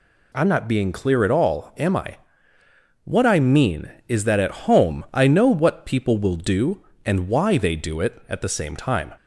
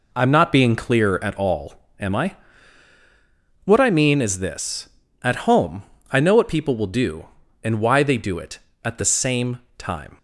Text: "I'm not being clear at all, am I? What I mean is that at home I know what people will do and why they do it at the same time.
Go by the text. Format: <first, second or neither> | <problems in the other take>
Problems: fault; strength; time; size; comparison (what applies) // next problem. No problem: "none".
first | says "this" for "that"; at 4.3 s // pauses between "home" and "I"; slight; at 5.8 s; 0.28 s long // pauses between "same" and "time"; slight; at 9.5 s; 0.18 s long